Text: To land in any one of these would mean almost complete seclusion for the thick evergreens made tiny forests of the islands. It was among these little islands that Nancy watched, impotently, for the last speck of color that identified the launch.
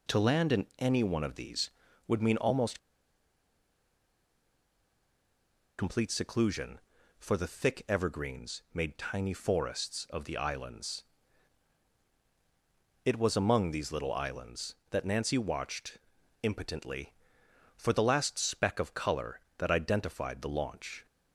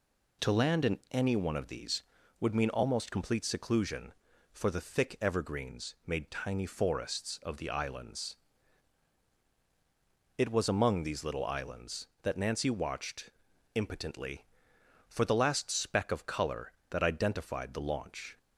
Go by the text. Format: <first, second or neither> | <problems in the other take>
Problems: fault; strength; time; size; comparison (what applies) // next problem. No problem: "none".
second | pauses between "almost" and "complete"; strong; at 2.7 s; 3.0 s long